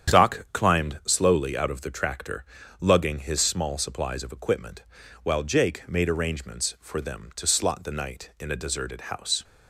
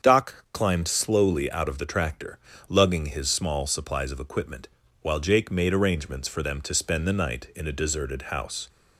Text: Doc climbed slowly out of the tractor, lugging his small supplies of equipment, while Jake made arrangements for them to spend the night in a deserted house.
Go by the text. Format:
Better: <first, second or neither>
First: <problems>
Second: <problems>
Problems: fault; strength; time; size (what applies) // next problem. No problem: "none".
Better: second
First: starts louder than the rest; strong; until 1.2 s; 8.5 dB // says "slot" for "spend"; at 7.4 s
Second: starts louder than the rest; until 1.1 s; 7 dB